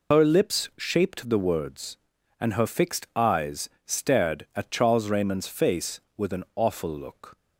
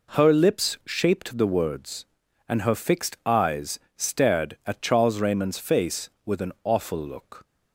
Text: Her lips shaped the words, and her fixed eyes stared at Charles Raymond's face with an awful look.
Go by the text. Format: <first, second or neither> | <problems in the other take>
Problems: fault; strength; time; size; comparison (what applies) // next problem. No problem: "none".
second | loses the start of "Her"; at 0.1 s; 105 ms // pauses between "eyes" and "stared"; slight; at 3.6 s; 0.17 s long; slight in the second